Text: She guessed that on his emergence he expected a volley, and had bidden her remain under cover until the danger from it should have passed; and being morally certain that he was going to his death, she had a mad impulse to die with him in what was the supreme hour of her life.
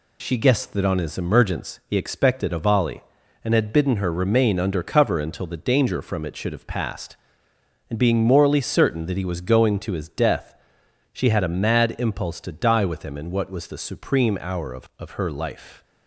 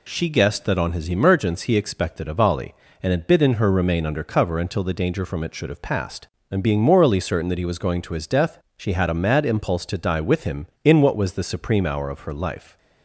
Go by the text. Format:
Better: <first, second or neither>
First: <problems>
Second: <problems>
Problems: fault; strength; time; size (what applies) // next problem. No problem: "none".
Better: second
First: says "of" twice; at 14.9 s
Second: none